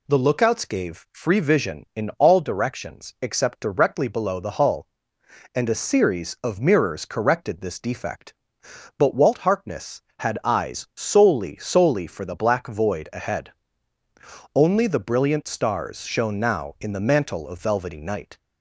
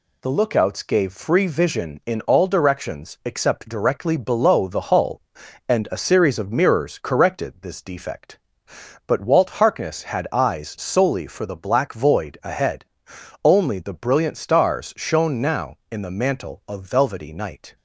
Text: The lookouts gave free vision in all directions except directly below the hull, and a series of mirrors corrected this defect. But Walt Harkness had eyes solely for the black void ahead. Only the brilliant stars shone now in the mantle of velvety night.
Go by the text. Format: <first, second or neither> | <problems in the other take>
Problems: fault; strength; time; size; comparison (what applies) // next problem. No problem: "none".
second | says "solely" twice; at 11.5 s